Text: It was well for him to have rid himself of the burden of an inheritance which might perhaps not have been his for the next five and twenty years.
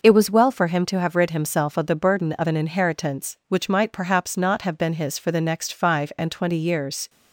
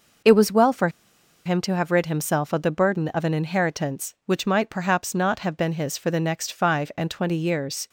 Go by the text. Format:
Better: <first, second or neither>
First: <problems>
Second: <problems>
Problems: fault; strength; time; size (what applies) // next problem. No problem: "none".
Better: first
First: none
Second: pauses between "for" and "him"; noticeable; at 0.8 s; 0.56 s long